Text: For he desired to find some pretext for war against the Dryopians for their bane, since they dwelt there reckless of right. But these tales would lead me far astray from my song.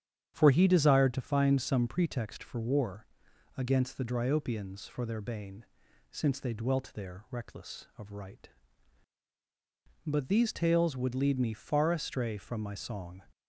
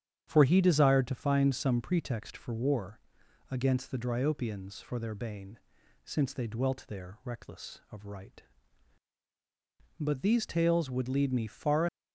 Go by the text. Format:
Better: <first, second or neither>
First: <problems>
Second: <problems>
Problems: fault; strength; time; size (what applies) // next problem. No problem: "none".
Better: first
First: starts louder than the rest; strong; until 1.3 s; 9 dB // pauses between "war" and "against"; noticeable; at 3.0 s; 0.50 s long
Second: starts louder than the rest; strong; until 1.2 s; 9 dB // pauses between "war" and "against"; noticeable; at 3.0 s; 0.50 s long // stops before "astray from my song"; at 11.8 s